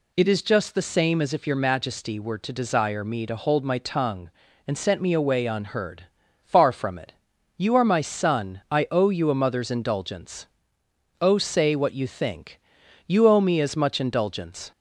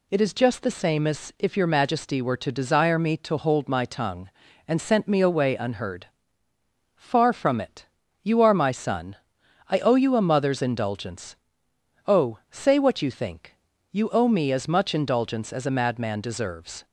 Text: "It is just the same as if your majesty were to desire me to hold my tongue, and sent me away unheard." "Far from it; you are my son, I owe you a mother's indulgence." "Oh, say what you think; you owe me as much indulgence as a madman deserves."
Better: second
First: stops before "as a madman deserves"; at 14.7 s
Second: none

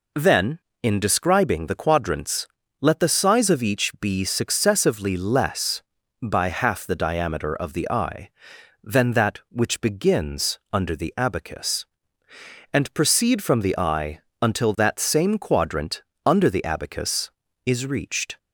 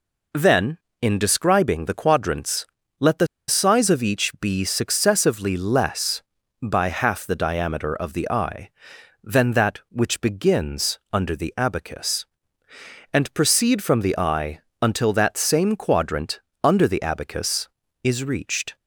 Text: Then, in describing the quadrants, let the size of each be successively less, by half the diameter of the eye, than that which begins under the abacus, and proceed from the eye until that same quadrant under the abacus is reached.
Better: first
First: pauses between "eye" and "until"; slight; at 14.1 s; 0.22 s long // pauses between "quadrant" and "under"; slight; at 16.0 s; 0.24 s long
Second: pauses between "the" and "size"; slight; at 3.2 s; 0.22 s long // pauses between "eye" and "until"; slight; at 14.5 s; 0.22 s long // pauses between "quadrant" and "under"; slight; at 16.3 s; 0.24 s long

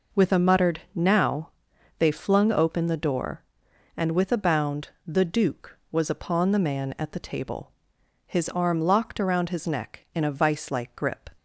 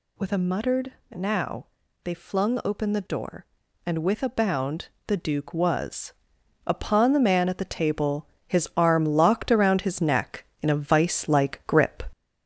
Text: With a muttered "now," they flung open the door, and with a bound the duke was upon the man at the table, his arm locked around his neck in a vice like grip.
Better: first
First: pauses between "bound" and "the"; slight; at 4.8 s; 0.18 s long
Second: gets louder; throughout; 3.5 dB // pauses between "muttered" and "now"; slight; at 0.9 s; 0.18 s long // pauses between "bound" and "the"; slight; at 4.8 s; 0.18 s long // pauses between "was" and "upon"; noticeable; at 6.1 s; 0.56 s long

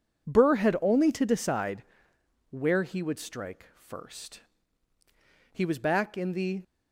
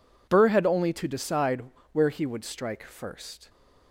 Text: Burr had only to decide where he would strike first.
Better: second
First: pauses between "decide" and "where"; noticeable; at 1.8 s; 0.68 s long // goes on to say "He was back in the"; noticeable; from 5.5 s on; 1.1 s long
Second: pauses between "decide" and "where"; slight; at 1.6 s; 0.28 s long

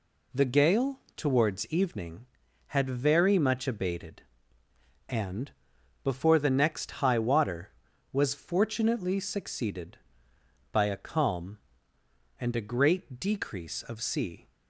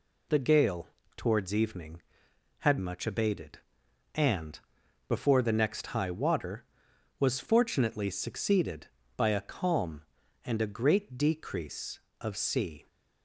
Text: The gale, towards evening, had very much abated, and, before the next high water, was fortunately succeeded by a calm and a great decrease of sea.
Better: first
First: none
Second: skips "very"; at 2.7 s

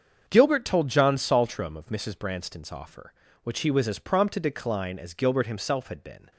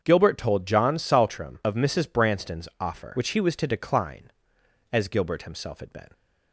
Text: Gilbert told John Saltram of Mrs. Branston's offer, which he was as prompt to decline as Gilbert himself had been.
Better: first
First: starts louder than the rest; until 1.2 s; 7 dB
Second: starts louder than the rest; until 1.0 s; 7 dB // skips "as prompt"; at 3.5 s

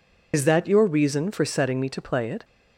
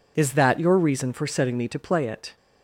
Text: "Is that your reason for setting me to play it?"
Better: second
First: loses the start of "Is"; at 0.3 s; 90 ms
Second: none

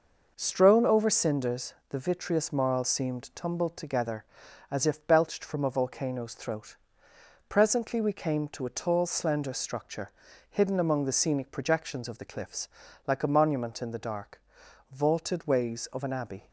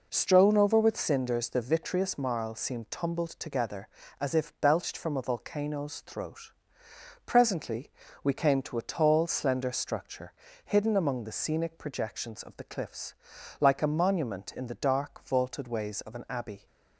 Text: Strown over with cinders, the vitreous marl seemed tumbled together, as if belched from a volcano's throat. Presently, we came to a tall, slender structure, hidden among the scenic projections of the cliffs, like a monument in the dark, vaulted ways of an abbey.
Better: second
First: skips "with"; at 1.1 s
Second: none

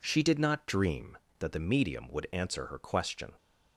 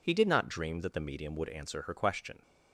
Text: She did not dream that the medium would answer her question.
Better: first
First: none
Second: says "He" for "She"; at 0.0 s

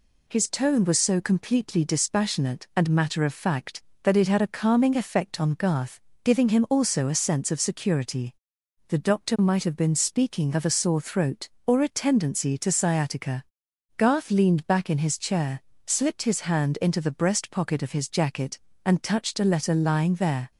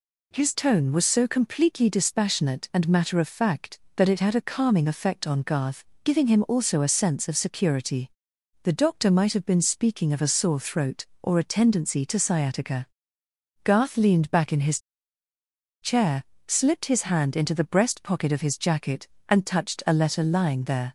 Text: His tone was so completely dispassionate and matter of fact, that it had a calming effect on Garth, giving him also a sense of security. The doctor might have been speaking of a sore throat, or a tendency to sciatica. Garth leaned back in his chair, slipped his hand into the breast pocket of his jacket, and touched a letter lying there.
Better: first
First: none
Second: pauses between "his" and "chair"; at 14.7 s; 1.0 s long

